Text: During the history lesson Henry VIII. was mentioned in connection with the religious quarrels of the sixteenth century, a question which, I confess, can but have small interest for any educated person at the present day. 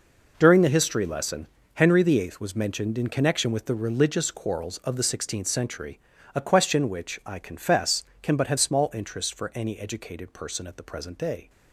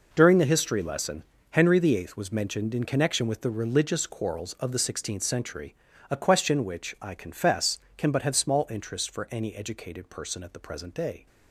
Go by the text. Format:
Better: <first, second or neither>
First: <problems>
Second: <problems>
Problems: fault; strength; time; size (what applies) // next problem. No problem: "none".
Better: neither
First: pauses between "lesson" and "Henry"; slight; at 1.4 s; 0.28 s long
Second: pauses between "lesson" and "Henry"; slight; at 1.2 s; 0.28 s long